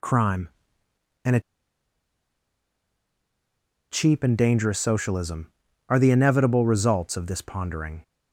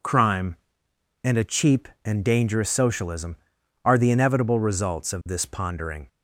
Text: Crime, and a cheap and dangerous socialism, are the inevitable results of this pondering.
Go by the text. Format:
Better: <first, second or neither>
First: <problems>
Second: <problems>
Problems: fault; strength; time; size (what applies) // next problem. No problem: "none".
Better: second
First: pauses between "a" and "cheap"; strong; at 1.3 s; 2.5 s long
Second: none